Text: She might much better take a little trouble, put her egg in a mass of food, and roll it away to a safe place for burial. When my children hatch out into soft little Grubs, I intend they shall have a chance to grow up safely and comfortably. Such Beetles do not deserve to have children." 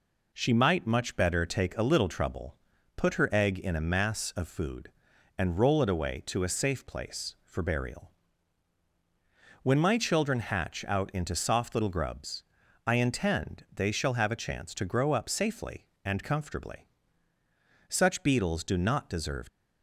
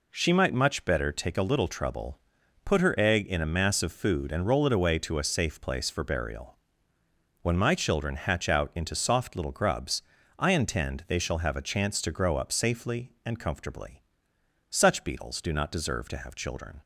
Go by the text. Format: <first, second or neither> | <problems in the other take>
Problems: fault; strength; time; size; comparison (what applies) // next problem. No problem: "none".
second | stops before "to have children"; at 19.4 s